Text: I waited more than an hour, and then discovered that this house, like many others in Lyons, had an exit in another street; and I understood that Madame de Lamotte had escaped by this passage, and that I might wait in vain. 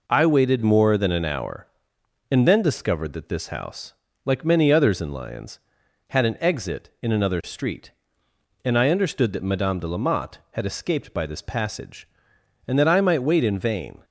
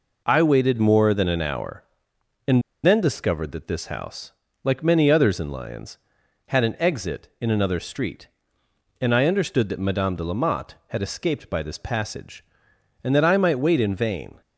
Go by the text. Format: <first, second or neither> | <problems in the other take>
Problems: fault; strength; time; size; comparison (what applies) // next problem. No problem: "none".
first | pauses between "and" and "then"; slight; at 2.6 s; 0.23 s long